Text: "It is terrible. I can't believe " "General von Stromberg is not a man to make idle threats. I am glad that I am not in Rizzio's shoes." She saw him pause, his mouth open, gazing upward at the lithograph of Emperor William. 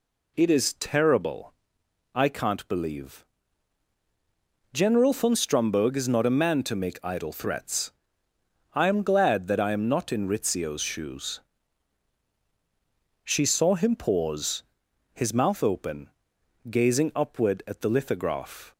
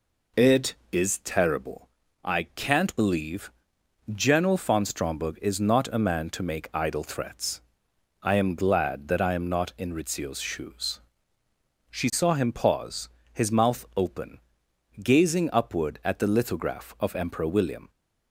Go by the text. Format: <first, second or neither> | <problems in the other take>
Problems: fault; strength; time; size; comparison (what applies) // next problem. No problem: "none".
second | stops before "of Emperor William"; at 18.7 s